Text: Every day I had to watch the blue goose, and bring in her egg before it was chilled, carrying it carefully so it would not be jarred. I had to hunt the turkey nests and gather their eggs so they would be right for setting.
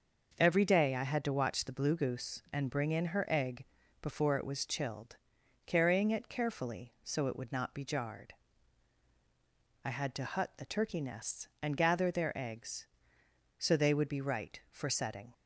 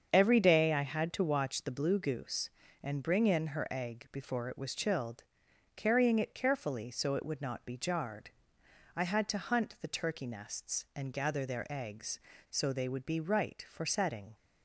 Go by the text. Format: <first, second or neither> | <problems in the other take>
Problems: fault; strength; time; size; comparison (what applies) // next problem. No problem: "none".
second | starts louder than the rest; noticeable; until 1.3 s; 6 dB; also in the second // pauses between "egg" and "before"; slight; at 3.6 s; 0.36 s long // says "hut" for "hunt"; at 10.2 s